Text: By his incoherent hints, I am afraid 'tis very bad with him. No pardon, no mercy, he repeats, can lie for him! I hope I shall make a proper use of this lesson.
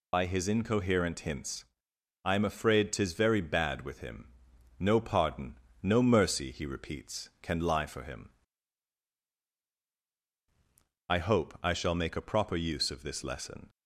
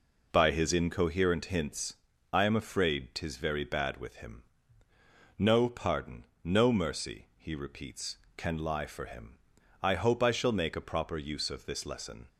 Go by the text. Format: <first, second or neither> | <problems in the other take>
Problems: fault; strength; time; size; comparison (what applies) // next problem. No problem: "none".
second | loses the start of "By"; at 0.1 s; 40 ms